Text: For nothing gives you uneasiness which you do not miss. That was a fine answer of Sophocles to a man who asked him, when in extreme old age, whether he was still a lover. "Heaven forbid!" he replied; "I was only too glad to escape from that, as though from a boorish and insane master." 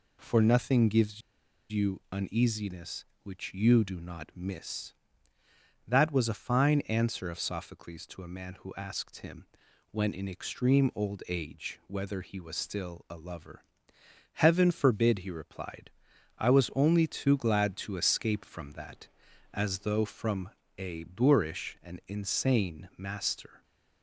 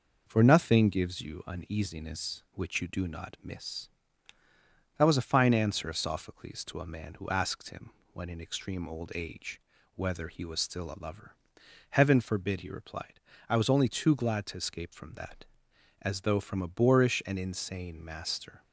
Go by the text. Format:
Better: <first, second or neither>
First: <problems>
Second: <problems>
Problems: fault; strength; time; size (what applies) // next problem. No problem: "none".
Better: second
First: pauses between "gives" and "you"; noticeable; at 1.2 s; 0.51 s long // pauses between "from" and "a"; slight; at 20.5 s; 0.26 s long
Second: none